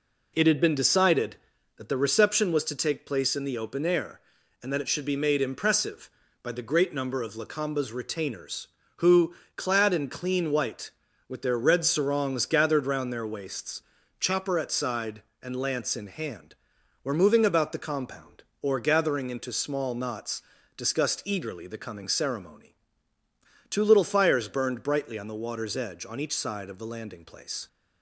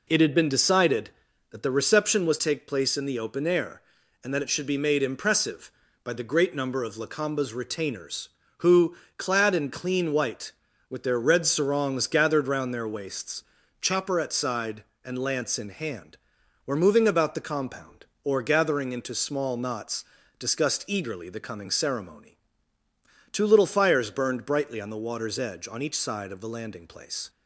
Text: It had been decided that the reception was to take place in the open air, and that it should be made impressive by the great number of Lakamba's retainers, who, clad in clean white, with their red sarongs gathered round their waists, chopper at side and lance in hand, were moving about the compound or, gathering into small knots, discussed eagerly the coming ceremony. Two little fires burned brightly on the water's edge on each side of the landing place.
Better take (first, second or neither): first